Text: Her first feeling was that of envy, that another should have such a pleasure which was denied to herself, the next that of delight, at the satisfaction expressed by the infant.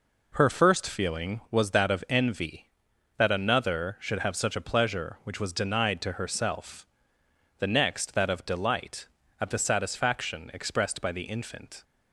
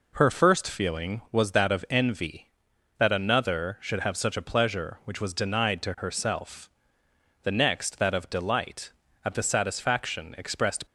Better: first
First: none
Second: stops before "by the infant"; at 10.8 s

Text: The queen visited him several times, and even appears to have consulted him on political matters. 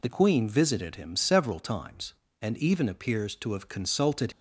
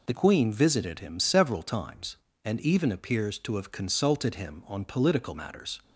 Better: second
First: stops before "him on political matters"; at 4.3 s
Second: none

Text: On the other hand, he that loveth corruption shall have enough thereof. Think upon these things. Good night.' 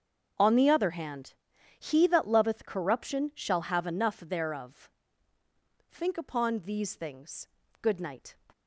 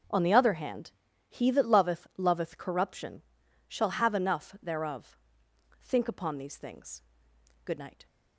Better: first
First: starts louder than the rest; until 1.8 s; 7 dB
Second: starts louder than the rest; until 1.4 s; 6.5 dB // says "loveth" twice; at 2.1 s // pauses between "corruption" and "shall"; noticeable; at 3.2 s; 0.46 s long

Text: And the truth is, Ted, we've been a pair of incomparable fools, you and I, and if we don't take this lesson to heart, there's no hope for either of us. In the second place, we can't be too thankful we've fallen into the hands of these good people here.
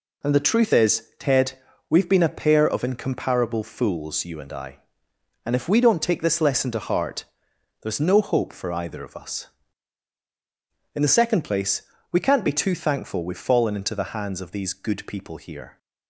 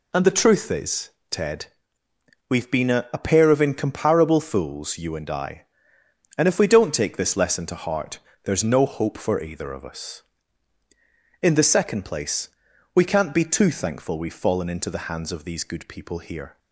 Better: first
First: none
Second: says "a" twice; at 3.1 s

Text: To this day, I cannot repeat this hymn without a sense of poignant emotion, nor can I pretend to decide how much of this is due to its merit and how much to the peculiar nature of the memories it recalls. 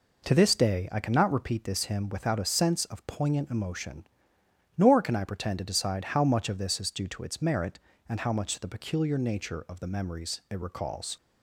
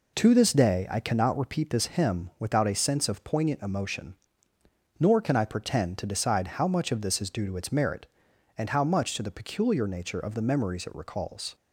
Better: neither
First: none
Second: none

